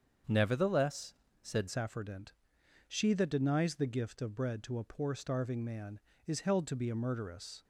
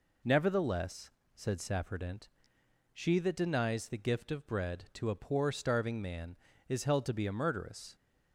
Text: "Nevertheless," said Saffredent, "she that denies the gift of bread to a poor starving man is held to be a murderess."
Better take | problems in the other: second | starts louder than the rest; until 1.5 s; 7 dB // changes voice at "Saffredent"; from 1.6 s on; 6.0 s long

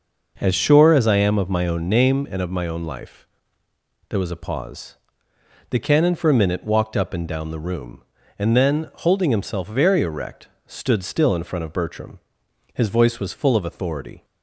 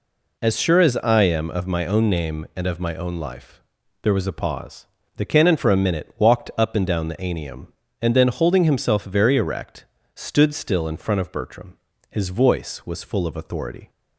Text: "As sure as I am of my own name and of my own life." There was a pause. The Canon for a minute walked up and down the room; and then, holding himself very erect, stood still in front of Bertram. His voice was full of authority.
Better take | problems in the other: first | says "anium" for "room"; at 7.1 s

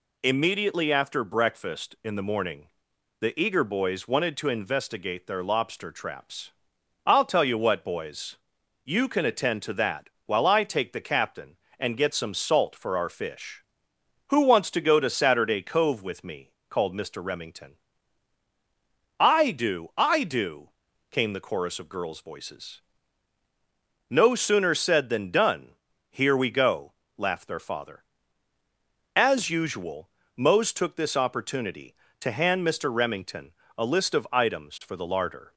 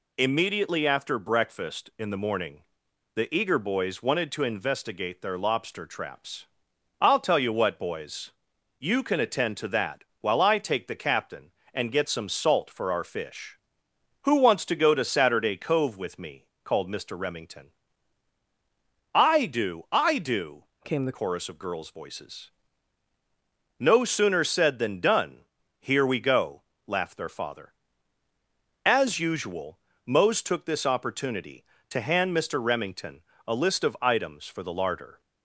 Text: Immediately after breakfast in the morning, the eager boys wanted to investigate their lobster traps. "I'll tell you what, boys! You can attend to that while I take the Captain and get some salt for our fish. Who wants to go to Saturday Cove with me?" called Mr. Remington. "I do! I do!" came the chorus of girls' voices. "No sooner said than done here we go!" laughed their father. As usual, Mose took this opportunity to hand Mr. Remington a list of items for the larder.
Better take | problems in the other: first | pauses between "that" and "while"; slight; at 10.0 s; 0.16 s long; slight in the first // changes voice from "came" to "the"; from 20.8 to 21.1 s; 0.3 s long // pauses between "done" and "here"; slight; at 25.4 s; 0.34 s long; slight in the first // pauses between "Remington" and "a"; slight; at 33.2 s; 0.24 s long; slight in the first

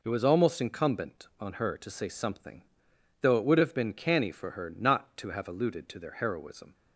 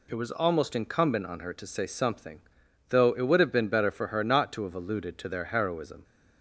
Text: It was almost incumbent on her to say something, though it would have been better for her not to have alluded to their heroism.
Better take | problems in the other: second | says "canny" for "better"; at 3.9 s

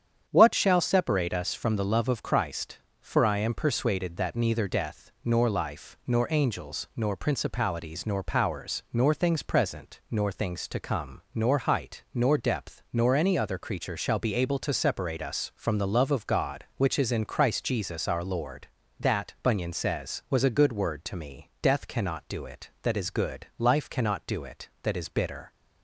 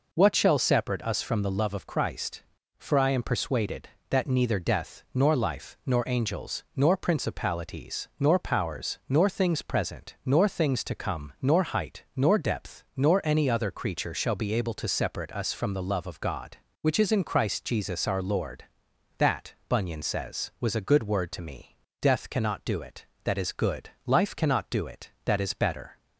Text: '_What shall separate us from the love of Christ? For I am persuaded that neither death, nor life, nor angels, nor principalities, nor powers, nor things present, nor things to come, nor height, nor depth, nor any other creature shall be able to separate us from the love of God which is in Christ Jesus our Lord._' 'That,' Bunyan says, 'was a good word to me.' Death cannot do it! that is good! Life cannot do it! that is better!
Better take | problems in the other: second | starts louder than the rest; strong; until 1.3 s; 8.5 dB // says "bitter" for "better"; at 25.0 s

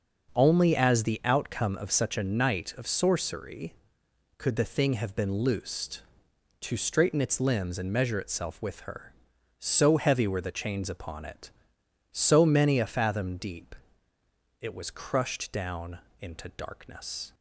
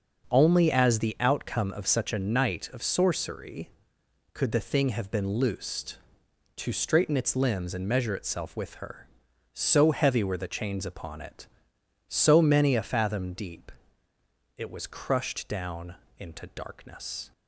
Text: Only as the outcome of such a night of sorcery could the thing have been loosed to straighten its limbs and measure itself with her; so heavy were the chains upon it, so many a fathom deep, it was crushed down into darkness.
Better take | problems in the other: neither | starts louder than the rest; the same in both // pauses between "down" and "into"; slight; the same in both

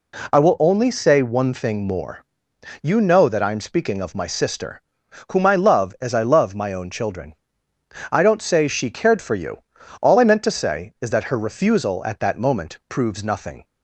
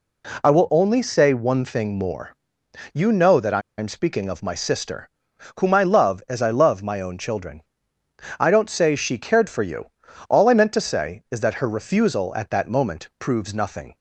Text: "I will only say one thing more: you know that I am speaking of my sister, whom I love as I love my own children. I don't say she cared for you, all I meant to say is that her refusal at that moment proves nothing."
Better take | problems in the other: first | pauses between "I" and "am"; slight; at 3.6 s; 0.16 s long

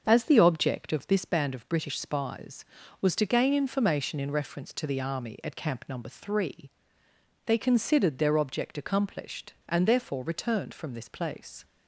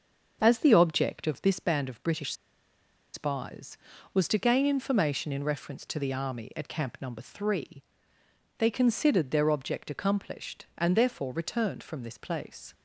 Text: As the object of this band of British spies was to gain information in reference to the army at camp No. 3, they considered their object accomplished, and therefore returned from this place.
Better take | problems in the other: first | starts louder than the rest; until 1.4 s; 6.5 dB; also in the first // pauses between "British" and "spies"; noticeable; at 2.3 s; 0.80 s long

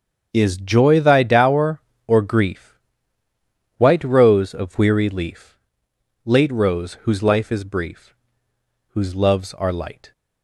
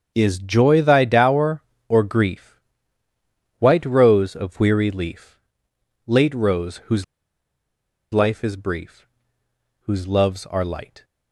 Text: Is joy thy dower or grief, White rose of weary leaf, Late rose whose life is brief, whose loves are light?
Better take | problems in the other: first | starts louder than the rest; until 1.1 s; 6.5 dB; also in the first // pauses between "whose" and "life"; at 7.0 s; 1.0 s long

